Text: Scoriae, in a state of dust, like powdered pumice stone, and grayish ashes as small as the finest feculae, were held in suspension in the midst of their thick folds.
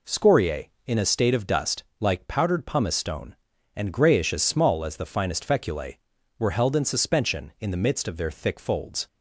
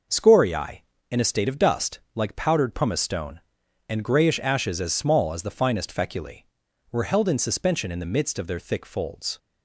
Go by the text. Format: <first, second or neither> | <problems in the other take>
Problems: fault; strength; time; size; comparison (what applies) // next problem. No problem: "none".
second | skips "ashes"; at 4.3 s